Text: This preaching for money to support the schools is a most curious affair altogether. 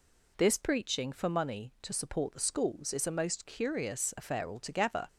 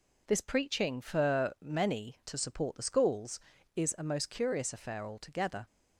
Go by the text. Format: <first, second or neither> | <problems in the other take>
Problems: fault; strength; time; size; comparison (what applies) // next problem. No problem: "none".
first | says "many" for "money"; at 1.5 s